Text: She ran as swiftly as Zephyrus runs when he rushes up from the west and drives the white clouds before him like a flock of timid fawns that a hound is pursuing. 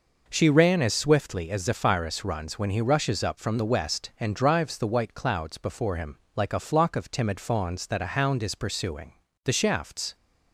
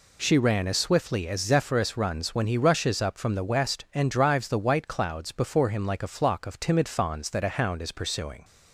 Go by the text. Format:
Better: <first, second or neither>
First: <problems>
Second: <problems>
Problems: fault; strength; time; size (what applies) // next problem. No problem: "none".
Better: second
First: pauses between "him" and "like"; slight; at 6.1 s; 0.16 s long // goes on to say "The shafts"; noticeable; from 9.4 s on; 0.70 s long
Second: none